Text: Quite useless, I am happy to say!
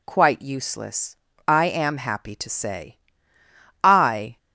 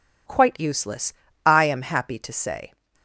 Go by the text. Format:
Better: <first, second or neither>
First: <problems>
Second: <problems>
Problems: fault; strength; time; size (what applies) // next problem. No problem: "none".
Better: second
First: goes on to say "I"; from 3.8 s on; 0.54 s long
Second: none